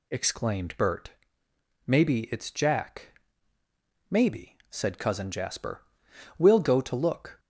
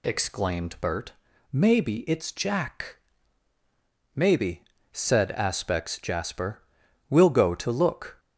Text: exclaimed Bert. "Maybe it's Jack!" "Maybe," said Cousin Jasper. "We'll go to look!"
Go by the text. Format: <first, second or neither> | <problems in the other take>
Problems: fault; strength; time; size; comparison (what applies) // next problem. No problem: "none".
first | says "Aspects" for "Cousin"; at 5.3 s